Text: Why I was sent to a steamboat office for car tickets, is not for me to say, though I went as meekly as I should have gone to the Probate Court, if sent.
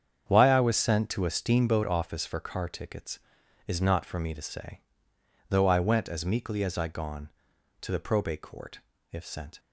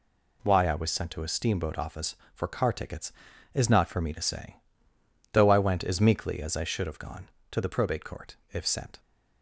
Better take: second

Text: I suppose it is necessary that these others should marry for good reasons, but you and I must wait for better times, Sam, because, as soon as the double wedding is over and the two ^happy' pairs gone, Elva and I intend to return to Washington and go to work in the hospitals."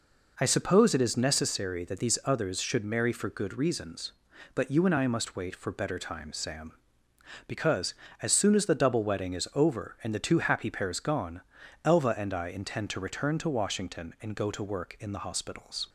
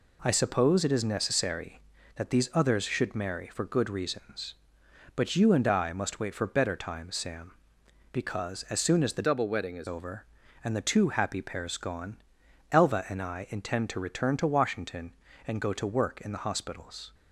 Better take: first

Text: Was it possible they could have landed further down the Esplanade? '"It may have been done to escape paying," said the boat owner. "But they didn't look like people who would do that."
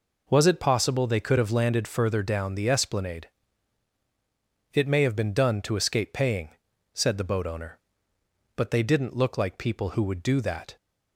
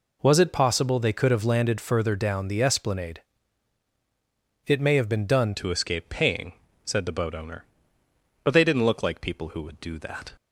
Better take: first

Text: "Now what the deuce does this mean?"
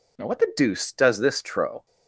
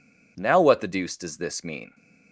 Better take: second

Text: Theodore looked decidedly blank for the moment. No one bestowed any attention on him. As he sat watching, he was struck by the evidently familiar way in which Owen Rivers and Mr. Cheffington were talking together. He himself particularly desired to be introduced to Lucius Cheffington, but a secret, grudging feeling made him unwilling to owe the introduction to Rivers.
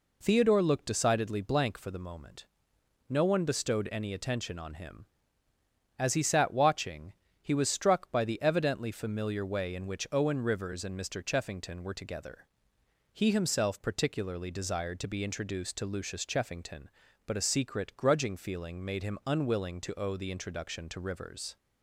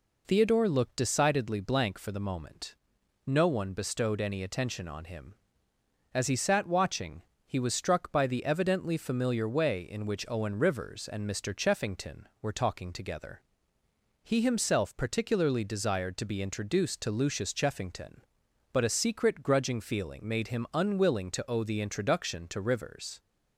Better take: second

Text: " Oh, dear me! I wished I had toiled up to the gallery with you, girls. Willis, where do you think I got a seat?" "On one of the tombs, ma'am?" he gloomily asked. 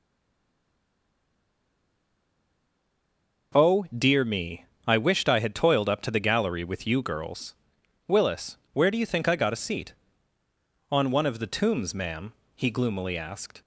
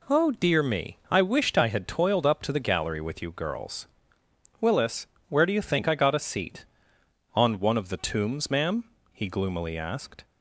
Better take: second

